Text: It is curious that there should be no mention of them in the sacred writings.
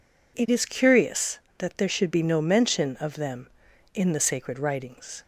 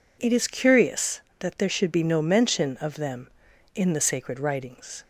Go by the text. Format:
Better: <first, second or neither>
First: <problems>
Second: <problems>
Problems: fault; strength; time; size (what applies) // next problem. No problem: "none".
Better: neither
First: none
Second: none